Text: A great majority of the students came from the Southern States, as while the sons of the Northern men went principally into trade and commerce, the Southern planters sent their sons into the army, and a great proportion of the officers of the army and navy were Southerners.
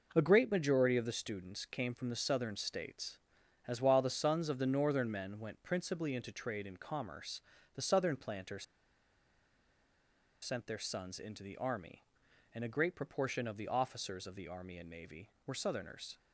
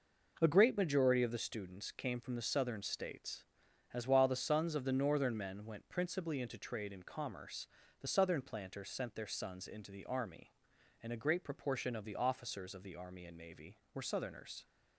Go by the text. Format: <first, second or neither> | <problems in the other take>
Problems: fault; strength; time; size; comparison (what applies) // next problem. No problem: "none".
second | pauses between "planters" and "sent"; strong; at 8.6 s; 1.7 s long